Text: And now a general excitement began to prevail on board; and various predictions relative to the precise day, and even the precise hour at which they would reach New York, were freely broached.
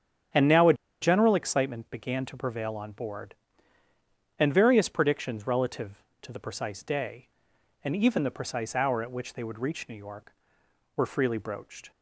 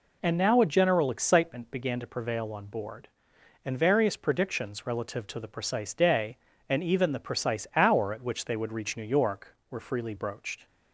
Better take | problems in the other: second | starts louder than the rest; strong; until 1.6 s; 8.5 dB // pauses between "a" and "general"; slight; at 0.7 s; 0.27 s long

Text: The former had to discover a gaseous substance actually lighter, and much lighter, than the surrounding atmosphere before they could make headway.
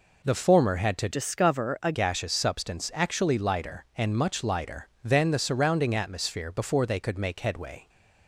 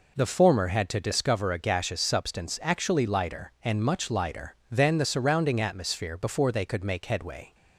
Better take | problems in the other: second | changes voice from "discover" to "a"; from 1.1 to 1.9 s; 0.8 s long

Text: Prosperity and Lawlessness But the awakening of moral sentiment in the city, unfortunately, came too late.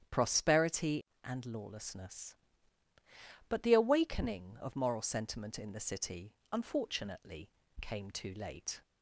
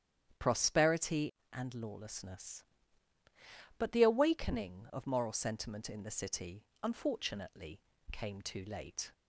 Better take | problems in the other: neither | starts louder than the rest; strong; the same in both

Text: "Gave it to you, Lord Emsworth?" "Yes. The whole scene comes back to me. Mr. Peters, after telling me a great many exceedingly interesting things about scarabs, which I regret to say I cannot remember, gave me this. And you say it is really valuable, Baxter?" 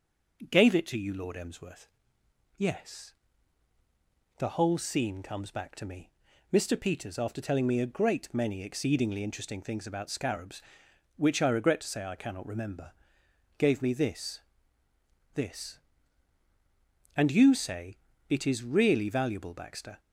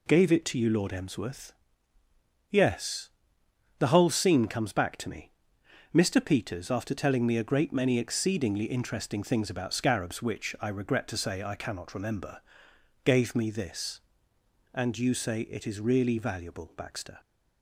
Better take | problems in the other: second | says "this" twice; at 15.3 s // pauses between "say" and "it"; slight; at 17.9 s; 0.30 s long

